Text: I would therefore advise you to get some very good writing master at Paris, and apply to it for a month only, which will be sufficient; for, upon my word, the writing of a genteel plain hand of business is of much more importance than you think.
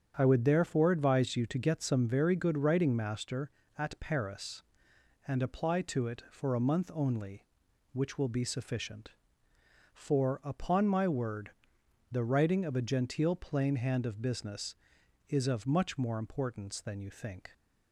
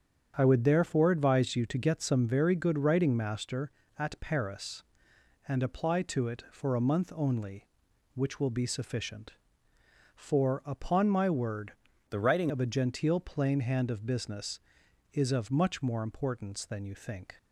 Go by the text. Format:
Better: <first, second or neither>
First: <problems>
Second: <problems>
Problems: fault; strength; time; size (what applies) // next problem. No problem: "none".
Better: first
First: starts louder than the rest; strong; until 1.1 s; 8 dB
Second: starts louder than the rest; strong; until 1.3 s; 8 dB // changes voice from "the" to "writing"; from 12.1 to 12.5 s; 0.4 s long